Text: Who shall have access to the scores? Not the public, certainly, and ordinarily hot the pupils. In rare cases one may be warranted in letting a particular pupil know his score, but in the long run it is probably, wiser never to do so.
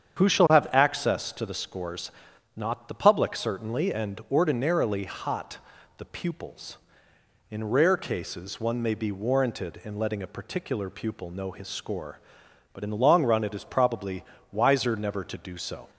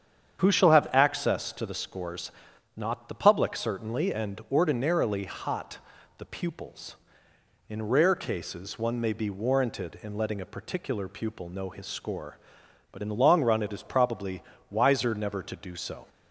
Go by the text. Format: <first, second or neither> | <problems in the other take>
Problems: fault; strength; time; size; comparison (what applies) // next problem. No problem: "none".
neither | starts louder than the rest; strong; the same in both // pauses between "hot" and "the"; the same in both